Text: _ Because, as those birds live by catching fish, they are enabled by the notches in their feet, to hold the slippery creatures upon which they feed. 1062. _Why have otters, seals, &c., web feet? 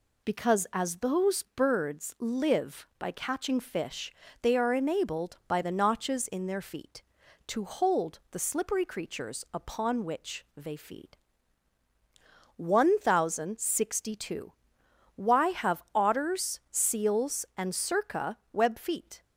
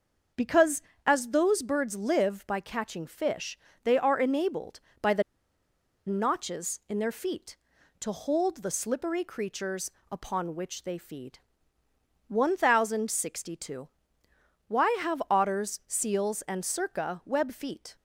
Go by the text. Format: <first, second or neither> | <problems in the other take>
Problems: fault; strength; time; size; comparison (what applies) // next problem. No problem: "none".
first | starts louder than the rest; noticeable; until 1.6 s; 6 dB // pauses between "the" and "notches"; noticeable; at 5.2 s; 0.84 s long // pauses between "creatures" and "upon"; slight; at 9.8 s; 0.22 s long